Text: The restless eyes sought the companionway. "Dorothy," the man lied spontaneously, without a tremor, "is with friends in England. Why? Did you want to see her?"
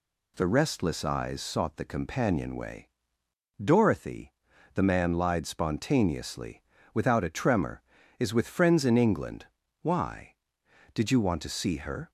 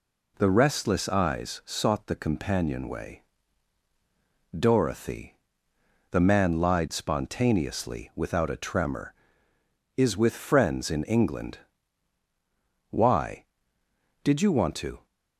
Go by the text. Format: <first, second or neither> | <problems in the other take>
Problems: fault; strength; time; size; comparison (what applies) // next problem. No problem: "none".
first | stops before "see her"; at 15.0 s